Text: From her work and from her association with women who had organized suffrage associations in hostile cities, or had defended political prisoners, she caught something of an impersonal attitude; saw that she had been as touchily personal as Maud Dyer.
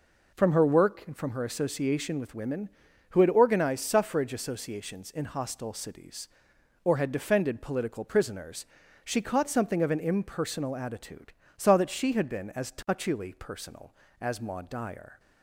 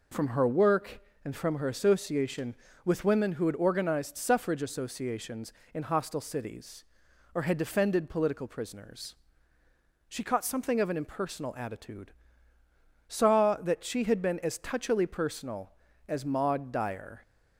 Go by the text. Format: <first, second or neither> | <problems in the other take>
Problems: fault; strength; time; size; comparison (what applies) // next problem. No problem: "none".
neither | none